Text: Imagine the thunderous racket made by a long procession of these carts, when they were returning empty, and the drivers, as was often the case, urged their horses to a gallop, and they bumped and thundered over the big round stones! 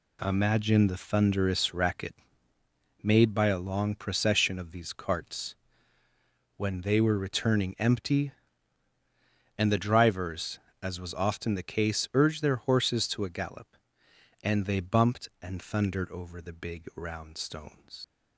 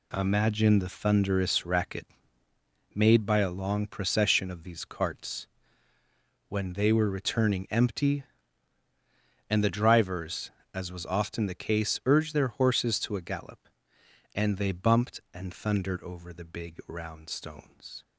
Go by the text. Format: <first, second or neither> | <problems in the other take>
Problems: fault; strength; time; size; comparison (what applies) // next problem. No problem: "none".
second | pauses between "racket" and "made"; noticeable; at 2.1 s; 0.88 s long; noticeable in the second // leaves "stones" unfinished; at 18.0 s; 75 ms